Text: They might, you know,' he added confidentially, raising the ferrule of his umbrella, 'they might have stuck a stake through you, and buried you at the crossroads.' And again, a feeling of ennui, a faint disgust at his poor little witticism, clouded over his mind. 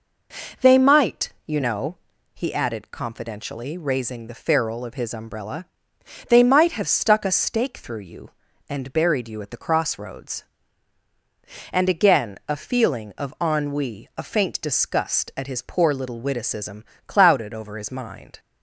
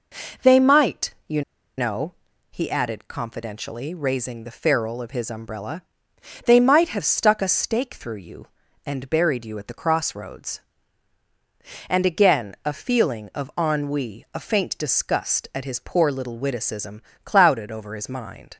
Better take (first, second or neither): first